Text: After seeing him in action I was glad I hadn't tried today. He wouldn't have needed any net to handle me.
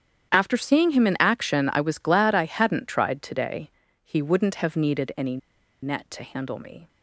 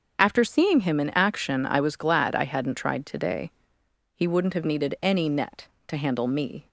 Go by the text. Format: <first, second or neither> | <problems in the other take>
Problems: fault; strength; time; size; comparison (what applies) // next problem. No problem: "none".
second | starts louder than the rest; strong; until 1.3 s; 9.5 dB; also in the second // pauses between "any" and "net"; at 5.3 s; 0.45 s long